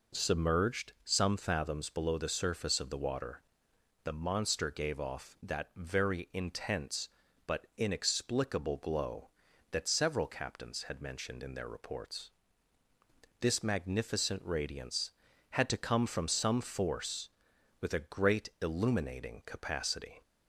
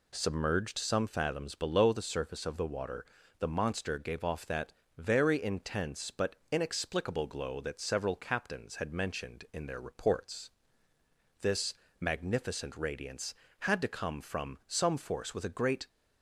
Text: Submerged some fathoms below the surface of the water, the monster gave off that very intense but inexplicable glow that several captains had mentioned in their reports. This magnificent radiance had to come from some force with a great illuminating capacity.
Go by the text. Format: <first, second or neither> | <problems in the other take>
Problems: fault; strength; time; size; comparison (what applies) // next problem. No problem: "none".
first | pauses between "that" and "very"; slight; at 4.7 s; 0.24 s long // pauses between "but" and "inexplicable"; slight; at 6.3 s; 0.16 s long // pauses between "This" and "magnificent"; slight; at 11.7 s; 0.26 s long // stops before "illuminating capacity"; at 15.8 s